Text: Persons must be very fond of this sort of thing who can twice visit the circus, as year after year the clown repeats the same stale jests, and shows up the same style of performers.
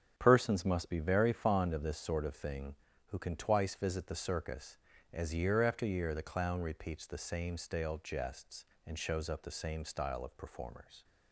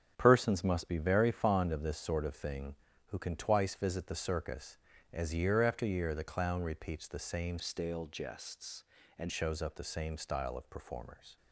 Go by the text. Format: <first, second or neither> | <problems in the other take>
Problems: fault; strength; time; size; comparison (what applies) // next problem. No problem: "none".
first | starts louder than the rest; strong; until 1.1 s; 7.5 dB; strong in the first // changes voice from "stale" to "and"; from 7.6 to 9.2 s; 1.6 s long